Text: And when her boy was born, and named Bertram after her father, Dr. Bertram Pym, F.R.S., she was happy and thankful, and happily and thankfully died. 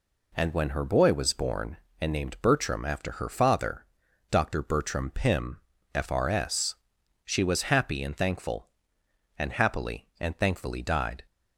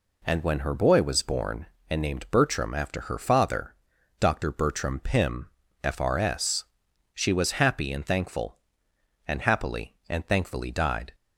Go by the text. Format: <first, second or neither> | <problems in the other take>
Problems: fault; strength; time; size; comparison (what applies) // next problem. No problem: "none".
neither | none